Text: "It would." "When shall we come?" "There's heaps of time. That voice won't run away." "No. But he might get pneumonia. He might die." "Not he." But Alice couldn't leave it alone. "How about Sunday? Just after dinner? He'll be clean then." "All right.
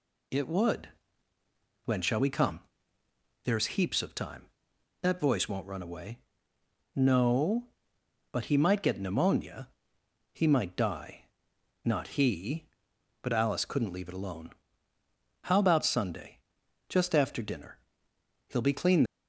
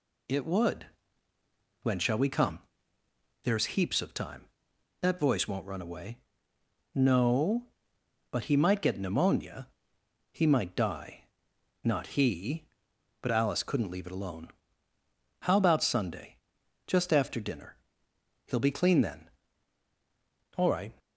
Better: second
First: stops before "then All right"; at 19.0 s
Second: none

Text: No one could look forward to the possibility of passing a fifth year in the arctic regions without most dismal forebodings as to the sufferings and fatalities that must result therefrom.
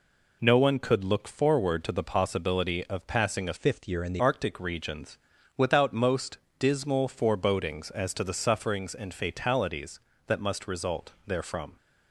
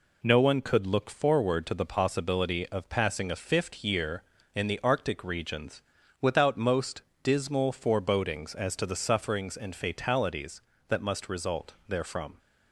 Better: second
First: changes voice from "fifth" to "the"; from 3.5 to 4.2 s; 0.7 s long // pauses between "regions" and "without"; at 5.1 s; 0.40 s long // pauses between "most" and "dismal"; slight; at 6.3 s; 0.20 s long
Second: pauses between "regions" and "without"; at 5.8 s; 0.40 s long // pauses between "most" and "dismal"; slight; at 7.0 s; 0.20 s long

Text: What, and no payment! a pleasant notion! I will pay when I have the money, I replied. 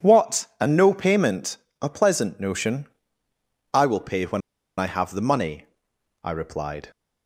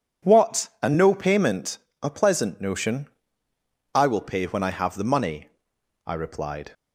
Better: second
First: pauses between "when" and "I"; at 4.4 s; 0.37 s long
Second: none

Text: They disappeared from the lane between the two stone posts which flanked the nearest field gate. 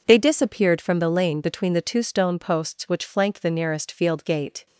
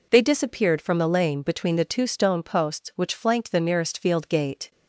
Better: neither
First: none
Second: none

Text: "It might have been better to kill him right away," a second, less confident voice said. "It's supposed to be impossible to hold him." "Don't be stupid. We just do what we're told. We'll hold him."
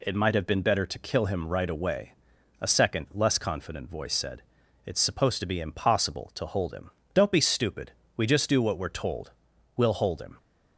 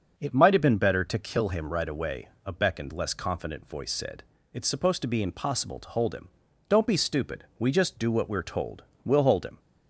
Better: first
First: none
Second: starts louder than the rest; until 1.1 s; 6 dB // says "beckoned" for "second"; at 2.5 s

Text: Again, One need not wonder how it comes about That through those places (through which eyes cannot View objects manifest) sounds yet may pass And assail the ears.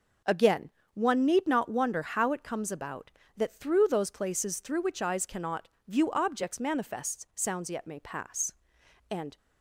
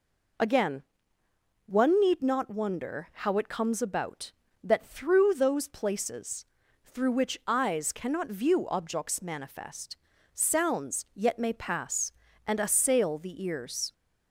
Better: second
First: pauses between "cannot" and "View"; slight; at 5.6 s; 0.22 s long // stops before "assail the ears"; at 9.3 s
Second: none

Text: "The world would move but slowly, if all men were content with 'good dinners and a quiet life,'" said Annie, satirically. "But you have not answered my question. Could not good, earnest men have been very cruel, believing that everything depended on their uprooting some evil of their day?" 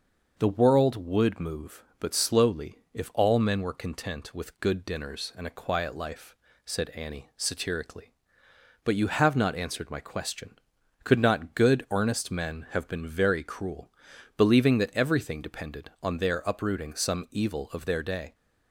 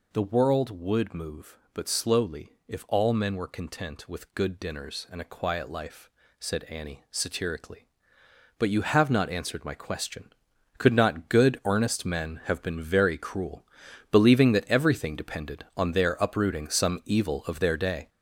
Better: first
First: none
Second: gets louder; throughout; 6.5 dB

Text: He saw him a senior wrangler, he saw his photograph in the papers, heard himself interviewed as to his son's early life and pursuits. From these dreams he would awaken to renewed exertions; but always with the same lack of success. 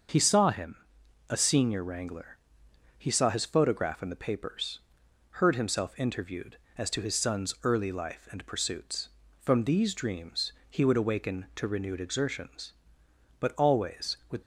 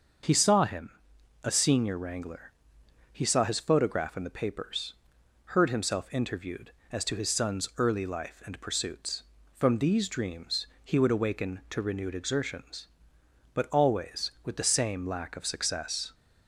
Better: second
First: starts louder than the rest; until 1.6 s; 6.5 dB // pauses between "him" and "a"; noticeable; at 0.7 s; 0.54 s long // pauses between "dreams" and "he"; slight; at 10.5 s; 0.16 s long // stops before "the same lack of success"; at 14.4 s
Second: starts louder than the rest; until 1.7 s; 6.5 dB // pauses between "him" and "a"; noticeable; at 0.8 s; 0.54 s long // pauses between "dreams" and "he"; slight; at 10.6 s; 0.16 s long

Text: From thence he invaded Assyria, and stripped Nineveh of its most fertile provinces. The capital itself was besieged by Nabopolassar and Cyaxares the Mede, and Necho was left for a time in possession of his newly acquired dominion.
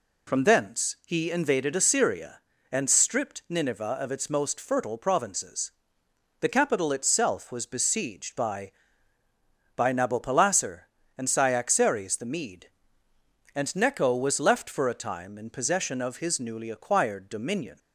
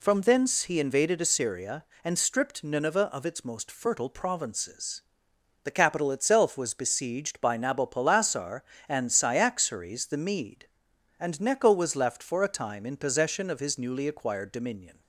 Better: second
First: says "by" twice; at 9.7 s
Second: none

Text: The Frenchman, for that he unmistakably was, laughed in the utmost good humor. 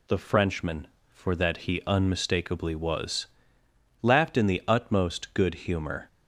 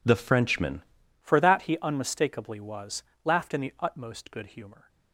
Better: first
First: none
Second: changes voice at "for"; from 1.2 s on; 3.6 s long

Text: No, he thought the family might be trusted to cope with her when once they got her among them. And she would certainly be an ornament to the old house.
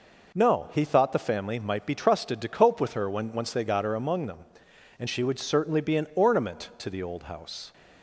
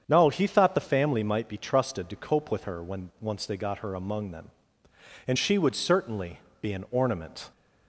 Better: first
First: none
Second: starts louder than the rest; strong; until 1.0 s; 8 dB // pauses between "certainly" and "be"; slight; at 6.3 s; 0.22 s long // stops before "to the old house"; at 7.5 s

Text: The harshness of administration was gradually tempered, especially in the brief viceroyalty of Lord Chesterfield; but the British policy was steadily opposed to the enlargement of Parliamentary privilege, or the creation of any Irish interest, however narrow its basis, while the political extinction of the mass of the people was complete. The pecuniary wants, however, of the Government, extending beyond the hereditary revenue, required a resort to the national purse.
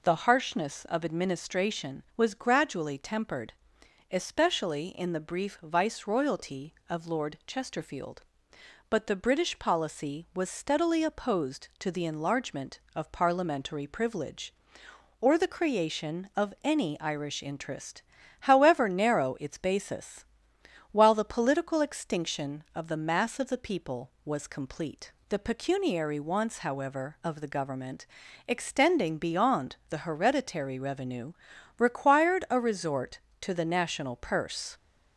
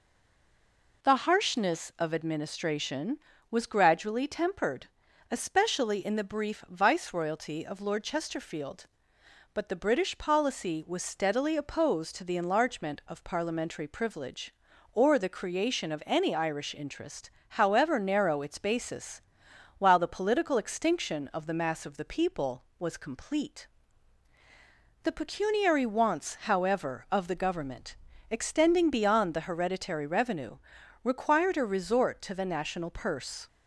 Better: first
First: none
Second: stays silent before the first word; until 1.0 s; 1.0 s long

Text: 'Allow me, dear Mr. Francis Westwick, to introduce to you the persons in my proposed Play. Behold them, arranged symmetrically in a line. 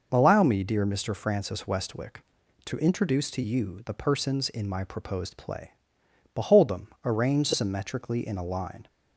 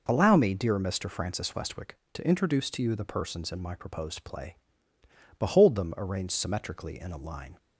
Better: neither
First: none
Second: none

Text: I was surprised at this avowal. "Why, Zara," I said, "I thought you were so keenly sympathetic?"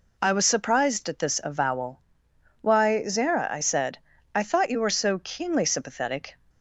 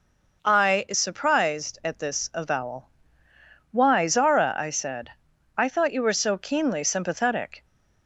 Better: first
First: none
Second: says "is" for "was"; at 0.8 s

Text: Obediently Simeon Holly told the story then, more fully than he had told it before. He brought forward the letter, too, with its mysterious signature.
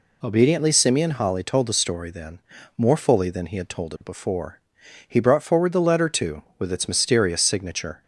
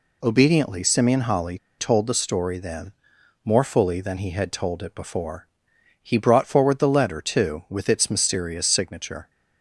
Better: first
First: none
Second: pauses between "Holly" and "told"; slight; at 1.5 s; 0.22 s long

